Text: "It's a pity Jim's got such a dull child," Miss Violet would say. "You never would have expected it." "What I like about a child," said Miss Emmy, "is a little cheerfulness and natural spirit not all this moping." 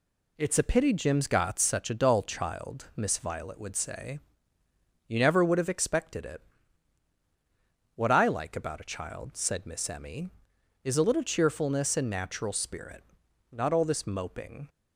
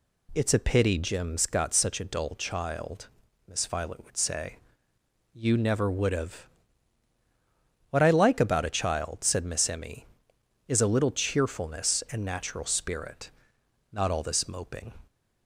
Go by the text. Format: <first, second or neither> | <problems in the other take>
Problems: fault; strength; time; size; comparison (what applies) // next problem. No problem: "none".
first | skips "expected it"; at 7.1 s // pauses between "spirit" and "not"; noticeable; at 13.3 s; 0.60 s long; noticeable in the first